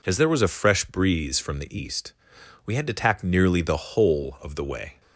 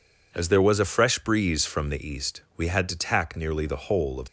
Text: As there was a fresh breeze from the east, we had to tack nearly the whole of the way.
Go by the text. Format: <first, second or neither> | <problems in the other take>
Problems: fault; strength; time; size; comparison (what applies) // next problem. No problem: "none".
first | stops before "the way"; at 4.2 s